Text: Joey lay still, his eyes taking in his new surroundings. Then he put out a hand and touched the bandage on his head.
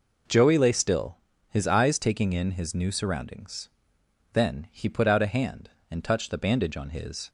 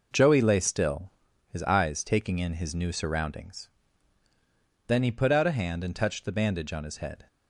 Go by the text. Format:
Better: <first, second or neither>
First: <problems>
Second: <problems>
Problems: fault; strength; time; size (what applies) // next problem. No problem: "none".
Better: second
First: stops before "head"; at 7.2 s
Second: none